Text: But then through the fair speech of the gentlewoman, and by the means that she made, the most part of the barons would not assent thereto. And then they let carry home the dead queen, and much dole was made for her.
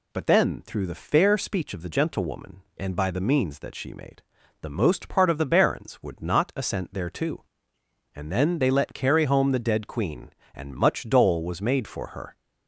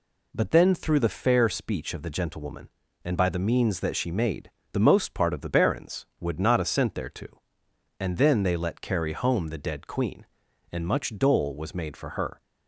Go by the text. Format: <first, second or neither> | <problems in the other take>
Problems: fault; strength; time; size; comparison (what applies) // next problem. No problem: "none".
neither | none